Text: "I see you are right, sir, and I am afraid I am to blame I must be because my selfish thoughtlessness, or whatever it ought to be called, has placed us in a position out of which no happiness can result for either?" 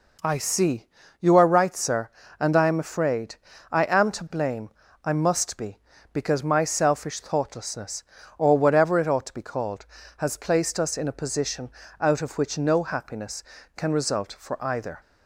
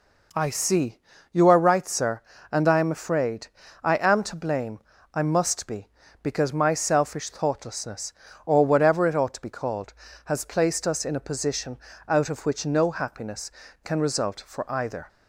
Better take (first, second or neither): neither